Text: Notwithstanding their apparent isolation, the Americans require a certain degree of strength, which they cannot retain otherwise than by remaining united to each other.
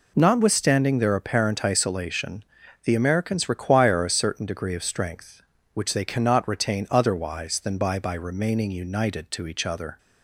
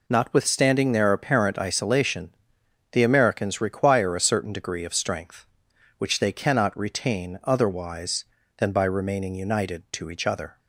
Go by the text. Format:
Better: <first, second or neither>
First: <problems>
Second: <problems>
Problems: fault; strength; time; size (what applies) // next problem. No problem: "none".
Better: second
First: says "by" twice; at 7.9 s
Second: none